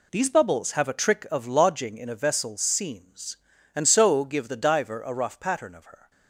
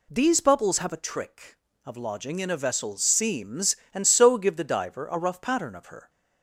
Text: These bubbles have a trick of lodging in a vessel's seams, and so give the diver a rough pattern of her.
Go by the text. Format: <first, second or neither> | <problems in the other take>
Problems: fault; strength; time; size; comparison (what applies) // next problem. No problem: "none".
neither | none